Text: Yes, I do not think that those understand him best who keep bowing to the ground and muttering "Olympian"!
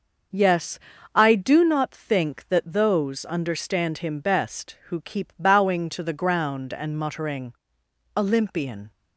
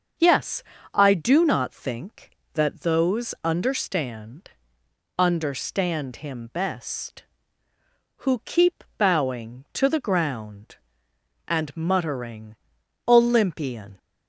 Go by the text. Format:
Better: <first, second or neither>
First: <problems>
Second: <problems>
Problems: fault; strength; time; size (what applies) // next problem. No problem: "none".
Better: first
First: starts louder than the rest; noticeable; until 1.6 s; 6 dB // pauses between "muttering" and "Olympian"; noticeable; at 7.5 s; 0.60 s long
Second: starts louder than the rest; until 1.4 s; 6.5 dB // says "understand" twice; at 5.1 s // pauses between "keep" and "bowing"; slight; at 8.8 s; 0.15 s long // pauses between "muttering" and "Olympian"; noticeable; at 12.5 s; 0.52 s long